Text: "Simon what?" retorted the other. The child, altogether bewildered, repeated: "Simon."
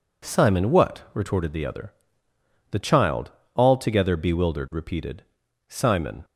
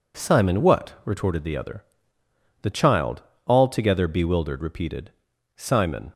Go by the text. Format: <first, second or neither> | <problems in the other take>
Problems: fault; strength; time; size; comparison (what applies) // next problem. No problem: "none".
neither | none